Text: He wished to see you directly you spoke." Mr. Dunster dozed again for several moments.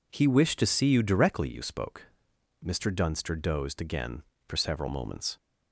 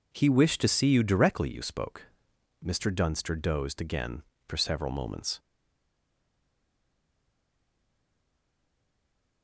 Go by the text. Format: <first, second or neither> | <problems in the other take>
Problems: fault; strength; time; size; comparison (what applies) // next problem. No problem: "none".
first | stays silent after the last word; strong; from 5.3 s on; 4.1 s long